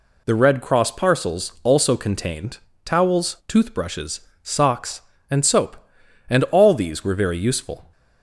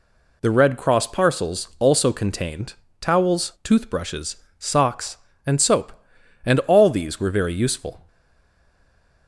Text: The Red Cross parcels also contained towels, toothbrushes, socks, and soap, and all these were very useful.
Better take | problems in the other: first | pauses between "contained" and "towels"; slight; at 2.7 s; 0.26 s long; slight in the first // stays silent after the last word; noticeable; from 8.0 s on; 1.2 s long

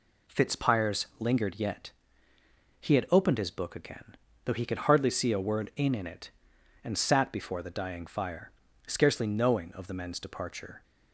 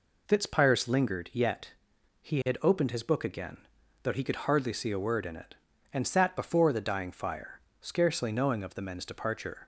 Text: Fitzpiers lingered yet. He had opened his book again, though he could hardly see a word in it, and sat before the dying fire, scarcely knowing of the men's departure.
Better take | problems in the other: second | says "in" twice; at 5.9 s

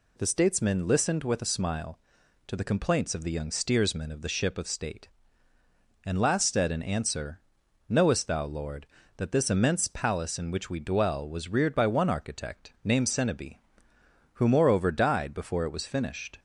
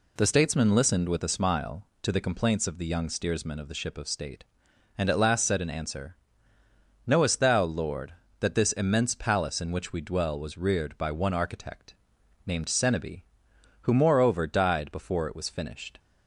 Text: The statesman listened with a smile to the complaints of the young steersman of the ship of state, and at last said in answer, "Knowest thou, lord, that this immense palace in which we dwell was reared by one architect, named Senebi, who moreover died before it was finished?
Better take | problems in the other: second | skips "at"; at 6.1 s

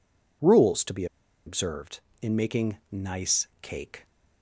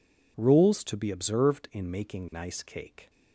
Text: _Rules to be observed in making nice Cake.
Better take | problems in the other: second | pauses between "be" and "observed"; at 1.0 s; 0.41 s long // pauses between "nice" and "Cake"; slight; at 3.4 s; 0.16 s long

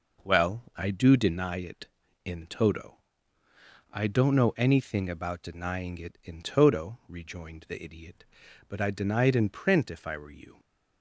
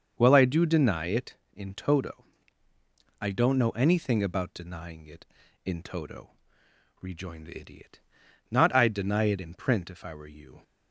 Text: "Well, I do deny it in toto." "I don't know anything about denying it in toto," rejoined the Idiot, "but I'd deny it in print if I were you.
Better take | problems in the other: first | starts louder than the rest; until 1.1 s; 6.5 dB // says "not" for "but"; at 8.4 s

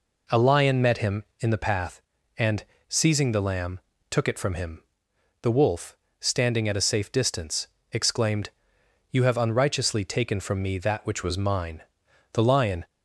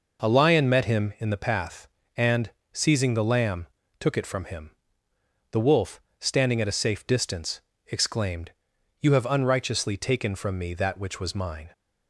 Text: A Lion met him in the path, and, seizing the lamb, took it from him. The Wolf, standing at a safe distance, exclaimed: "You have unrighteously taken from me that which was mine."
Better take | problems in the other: second | goes on to say "The Lion"; from 12.3 s on; 0.54 s long

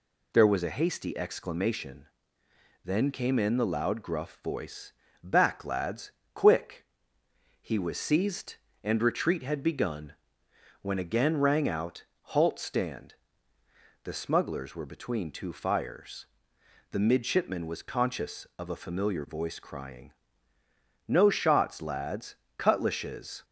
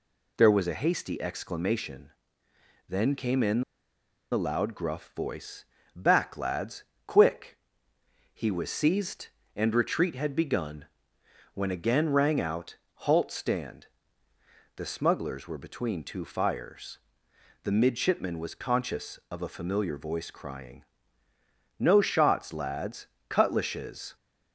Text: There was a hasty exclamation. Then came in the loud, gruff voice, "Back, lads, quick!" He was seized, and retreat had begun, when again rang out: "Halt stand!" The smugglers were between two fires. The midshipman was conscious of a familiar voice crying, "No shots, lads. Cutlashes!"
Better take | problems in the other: first | pauses between "in" and "the"; noticeable; at 3.6 s; 0.70 s long

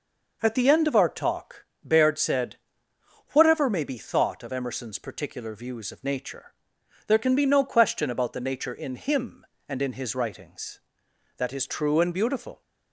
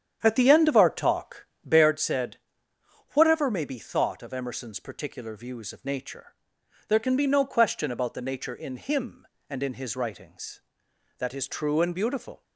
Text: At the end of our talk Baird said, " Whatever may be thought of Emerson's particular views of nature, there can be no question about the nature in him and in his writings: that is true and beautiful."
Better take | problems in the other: first | starts louder than the rest; strong; until 2.0 s; 8.5 dB // pauses between "talk" and "Baird"; slight; at 1.4 s; 0.18 s long; slight in the first

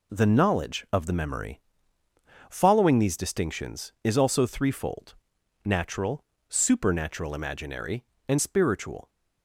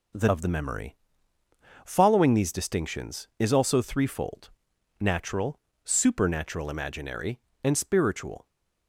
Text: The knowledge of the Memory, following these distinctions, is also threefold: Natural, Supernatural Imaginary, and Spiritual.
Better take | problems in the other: first | skips "knowledge"; at 0.2 s

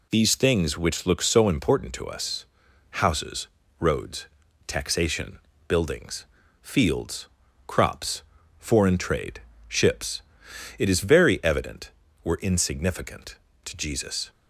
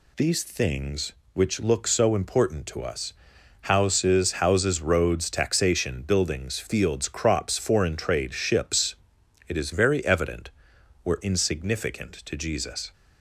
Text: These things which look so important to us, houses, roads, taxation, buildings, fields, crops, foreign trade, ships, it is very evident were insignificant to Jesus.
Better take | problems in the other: first | says "houses" twice; at 4.3 s

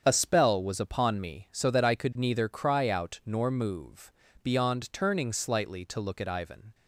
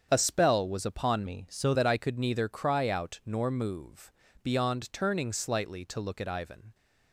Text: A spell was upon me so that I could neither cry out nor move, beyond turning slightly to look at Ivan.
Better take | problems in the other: first | starts louder than the rest; strong; until 1.1 s; 7.5 dB; strong in the first // changes voice from "me" to "so"; from 1.2 to 1.7 s; 0.5 s long

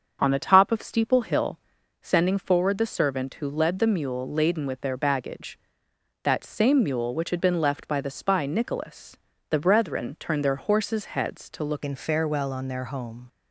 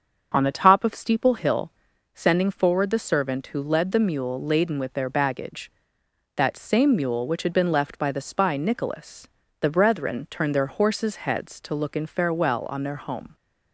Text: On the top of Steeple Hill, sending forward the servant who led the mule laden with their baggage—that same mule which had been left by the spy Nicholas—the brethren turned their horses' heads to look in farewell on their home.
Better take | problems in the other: second | starts louder than the rest; until 1.2 s; 7 dB; also in the second // changes voice at "in"; from 11.8 s on; 1.4 s long

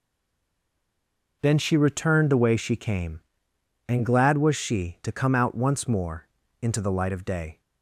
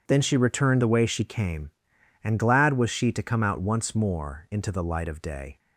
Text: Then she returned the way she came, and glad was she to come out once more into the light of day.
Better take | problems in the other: second | stays silent before the first word; noticeable; until 1.4 s; 1.4 s long // pauses between "more" and "into"; slight; at 6.2 s; 0.34 s long

